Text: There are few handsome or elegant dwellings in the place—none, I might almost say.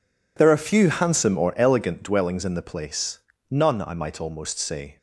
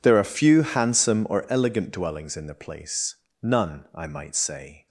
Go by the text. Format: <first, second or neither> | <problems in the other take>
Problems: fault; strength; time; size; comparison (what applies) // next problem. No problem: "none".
first | skips "almost"; at 4.3 s